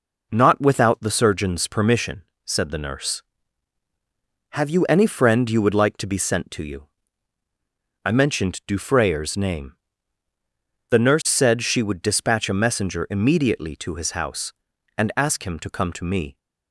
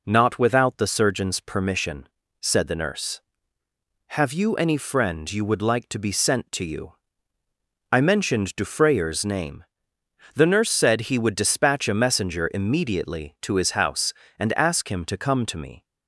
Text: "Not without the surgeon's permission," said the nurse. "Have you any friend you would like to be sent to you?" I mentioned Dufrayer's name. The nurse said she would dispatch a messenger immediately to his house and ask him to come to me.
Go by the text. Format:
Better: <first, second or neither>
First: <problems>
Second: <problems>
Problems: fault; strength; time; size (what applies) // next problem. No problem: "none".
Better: first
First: none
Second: says "he" for "she"; at 11.0 s